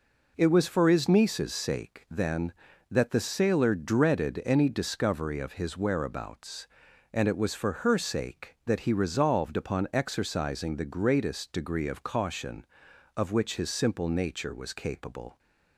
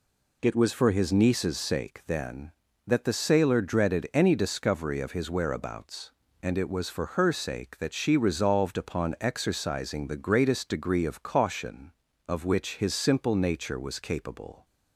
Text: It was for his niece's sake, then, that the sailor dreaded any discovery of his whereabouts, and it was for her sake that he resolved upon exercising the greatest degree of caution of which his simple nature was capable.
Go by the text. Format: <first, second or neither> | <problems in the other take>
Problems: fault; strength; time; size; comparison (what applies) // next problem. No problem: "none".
first | says "she" for "he"; at 7.9 s